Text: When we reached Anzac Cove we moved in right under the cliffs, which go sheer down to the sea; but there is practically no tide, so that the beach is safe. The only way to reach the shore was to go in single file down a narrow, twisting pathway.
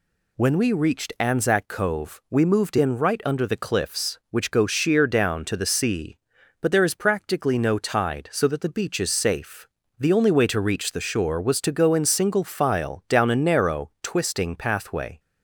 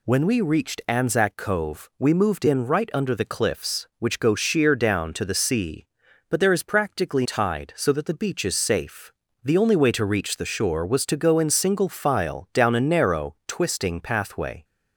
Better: first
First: none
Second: skips "no"; at 7.2 s

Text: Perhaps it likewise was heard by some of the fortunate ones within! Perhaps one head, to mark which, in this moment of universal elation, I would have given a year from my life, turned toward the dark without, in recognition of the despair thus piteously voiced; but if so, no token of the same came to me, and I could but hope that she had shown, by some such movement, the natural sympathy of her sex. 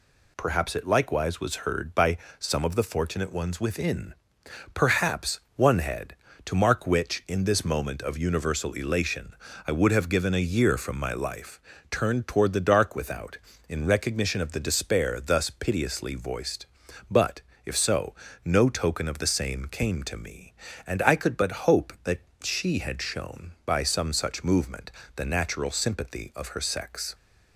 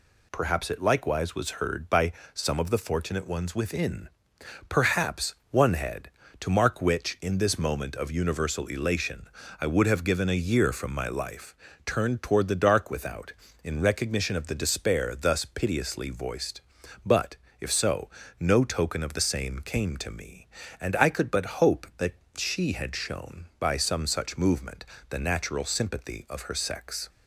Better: neither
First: pauses between "by" and "some"; slight; at 2.1 s; 0.20 s long // pauses between "Perhaps" and "one"; slight; at 5.3 s; 0.16 s long // pauses between "but" and "if"; slight; at 17.4 s; 0.22 s long // pauses between "that" and "she"; slight; at 22.2 s; 0.22 s long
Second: pauses between "by" and "some"; slight; at 2.1 s; 0.20 s long // pauses between "Perhaps" and "one"; slight; at 5.3 s; 0.16 s long // pauses between "but" and "if"; slight; at 17.3 s; 0.22 s long // pauses between "that" and "she"; slight; at 22.1 s; 0.22 s long

